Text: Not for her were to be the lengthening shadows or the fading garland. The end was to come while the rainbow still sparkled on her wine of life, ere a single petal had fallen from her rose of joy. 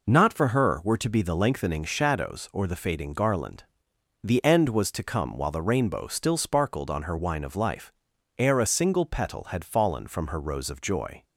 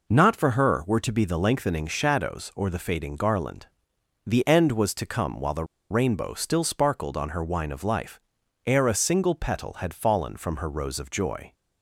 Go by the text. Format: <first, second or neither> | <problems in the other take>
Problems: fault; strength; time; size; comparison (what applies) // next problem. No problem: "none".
first | pauses between "the" and "rainbow"; slight; at 5.6 s; 0.25 s long